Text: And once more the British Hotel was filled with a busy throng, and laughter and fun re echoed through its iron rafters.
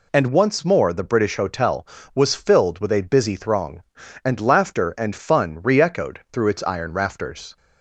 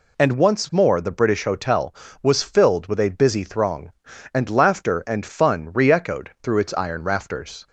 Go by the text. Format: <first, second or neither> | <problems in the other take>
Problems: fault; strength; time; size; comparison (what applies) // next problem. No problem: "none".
neither | none